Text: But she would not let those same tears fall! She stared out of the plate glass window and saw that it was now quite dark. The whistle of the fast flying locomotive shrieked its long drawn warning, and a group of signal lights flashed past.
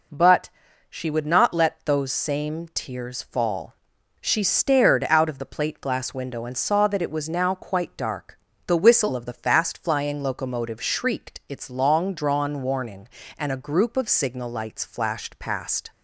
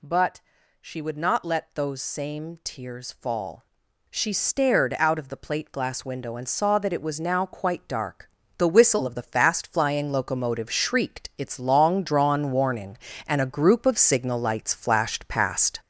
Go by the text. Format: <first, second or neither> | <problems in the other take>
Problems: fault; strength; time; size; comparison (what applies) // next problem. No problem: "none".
first | gets louder; throughout; 7 dB // pauses between "But" and "she"; at 0.3 s; 0.40 s long; also in the first